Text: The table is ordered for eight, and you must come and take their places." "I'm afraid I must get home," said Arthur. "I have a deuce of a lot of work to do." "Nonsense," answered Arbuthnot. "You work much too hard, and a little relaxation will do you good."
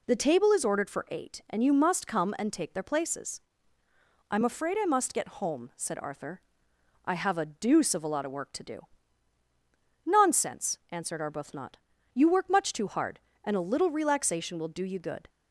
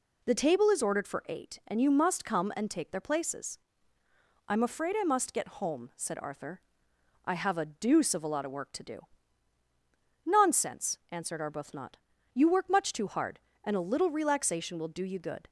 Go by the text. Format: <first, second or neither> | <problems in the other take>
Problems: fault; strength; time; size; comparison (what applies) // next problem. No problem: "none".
neither | none